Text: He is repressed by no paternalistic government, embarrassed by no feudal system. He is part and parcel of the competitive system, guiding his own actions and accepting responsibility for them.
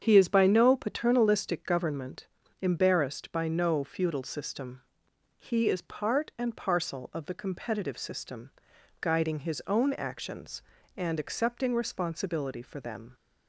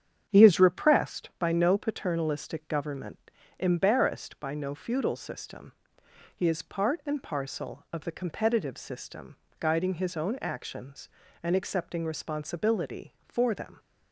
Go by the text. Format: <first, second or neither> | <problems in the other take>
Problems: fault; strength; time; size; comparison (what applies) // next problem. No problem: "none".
second | starts louder than the rest; strong; until 1.0 s; 8 dB; strong in the second // skips "repressed"; at 0.2 s